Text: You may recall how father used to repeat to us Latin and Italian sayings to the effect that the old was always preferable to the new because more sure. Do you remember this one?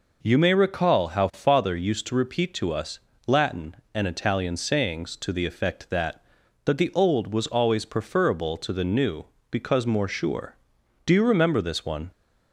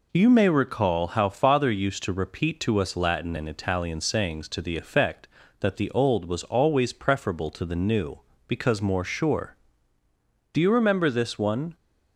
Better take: second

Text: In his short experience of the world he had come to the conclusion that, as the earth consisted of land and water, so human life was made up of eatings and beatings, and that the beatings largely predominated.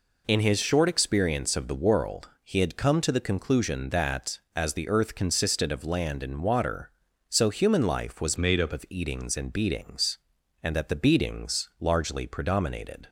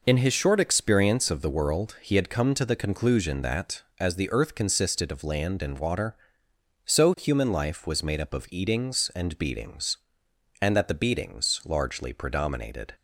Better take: second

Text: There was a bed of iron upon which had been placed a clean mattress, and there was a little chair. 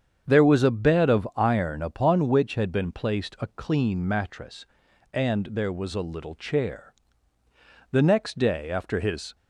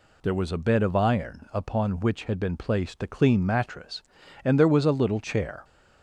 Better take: second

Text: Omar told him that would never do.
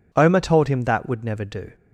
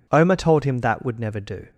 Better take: neither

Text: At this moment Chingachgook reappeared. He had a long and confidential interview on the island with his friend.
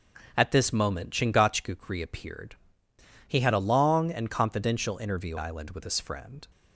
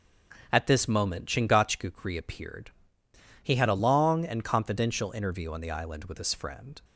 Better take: second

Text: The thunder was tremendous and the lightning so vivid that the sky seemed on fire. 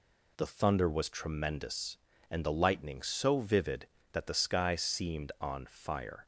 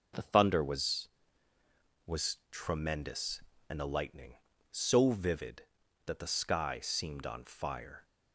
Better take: first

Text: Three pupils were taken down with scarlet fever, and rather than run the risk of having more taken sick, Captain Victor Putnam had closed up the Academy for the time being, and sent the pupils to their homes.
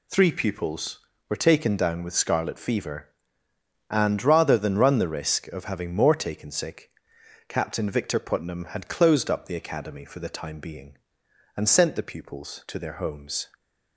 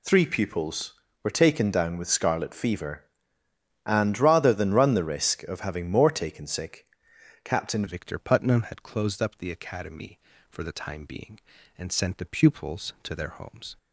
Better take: first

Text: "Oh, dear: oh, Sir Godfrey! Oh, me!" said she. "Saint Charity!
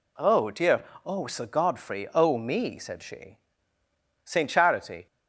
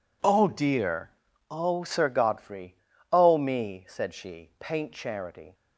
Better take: first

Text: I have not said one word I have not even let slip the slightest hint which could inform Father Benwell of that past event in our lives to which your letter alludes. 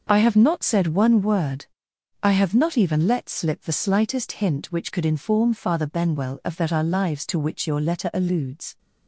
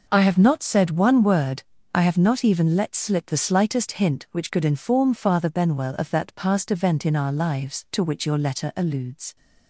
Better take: second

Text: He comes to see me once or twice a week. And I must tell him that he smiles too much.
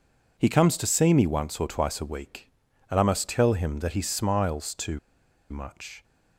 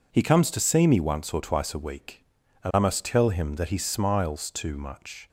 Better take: second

